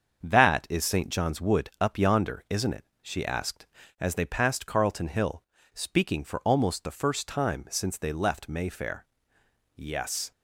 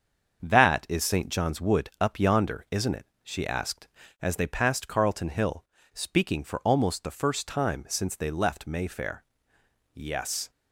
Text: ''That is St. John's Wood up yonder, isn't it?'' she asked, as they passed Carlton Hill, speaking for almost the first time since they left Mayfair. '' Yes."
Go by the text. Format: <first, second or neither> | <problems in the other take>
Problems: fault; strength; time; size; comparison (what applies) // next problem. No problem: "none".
neither | starts louder than the rest; the same in both